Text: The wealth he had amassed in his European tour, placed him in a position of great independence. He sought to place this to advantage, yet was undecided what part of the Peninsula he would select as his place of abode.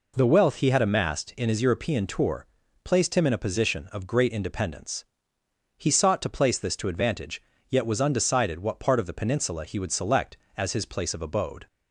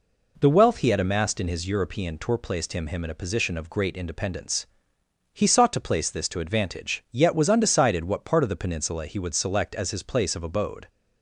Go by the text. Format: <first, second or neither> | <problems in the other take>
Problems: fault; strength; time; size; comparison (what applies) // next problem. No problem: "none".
first | says "him" twice; at 2.8 s